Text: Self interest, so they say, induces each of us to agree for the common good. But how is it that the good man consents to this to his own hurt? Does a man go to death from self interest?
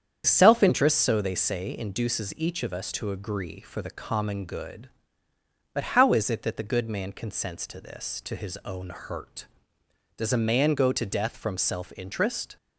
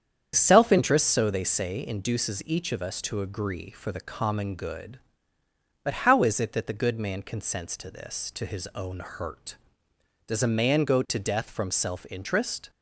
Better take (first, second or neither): neither